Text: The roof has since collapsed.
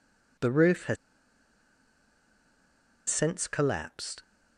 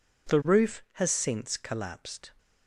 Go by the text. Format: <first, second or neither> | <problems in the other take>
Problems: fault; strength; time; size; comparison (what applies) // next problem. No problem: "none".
second | pauses between "has" and "since"; strong; at 0.9 s; 2.1 s long